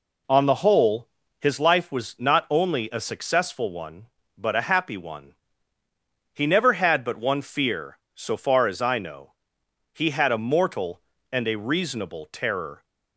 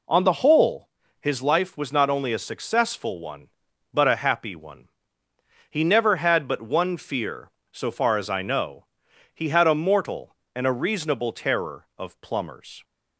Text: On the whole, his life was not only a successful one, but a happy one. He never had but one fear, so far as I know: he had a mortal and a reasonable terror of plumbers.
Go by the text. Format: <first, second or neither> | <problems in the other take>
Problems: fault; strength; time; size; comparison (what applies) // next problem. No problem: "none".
second | stops before "of plumbers"; at 12.8 s